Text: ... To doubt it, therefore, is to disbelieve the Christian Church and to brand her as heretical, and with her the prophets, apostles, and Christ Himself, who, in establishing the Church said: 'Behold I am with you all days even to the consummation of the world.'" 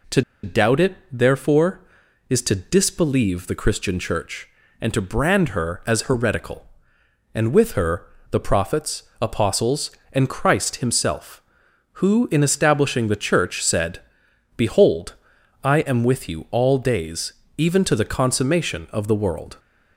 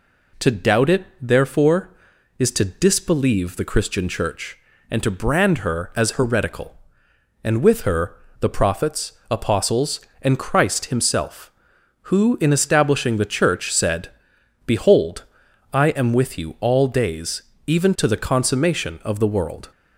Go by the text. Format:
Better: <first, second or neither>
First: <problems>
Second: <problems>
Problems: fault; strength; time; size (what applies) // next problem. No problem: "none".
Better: second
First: pauses between "To" and "doubt"; slight; at 0.2 s; 0.22 s long // pauses between "her" and "the"; slight; at 8.0 s; 0.24 s long // pauses between "Behold" and "I"; noticeable; at 15.1 s; 0.50 s long // pauses between "days" and "even"; slight; at 17.3 s; 0.26 s long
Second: pauses between "her" and "the"; slight; at 8.1 s; 0.24 s long // pauses between "Behold" and "I"; noticeable; at 15.2 s; 0.50 s long // pauses between "days" and "even"; slight; at 17.4 s; 0.26 s long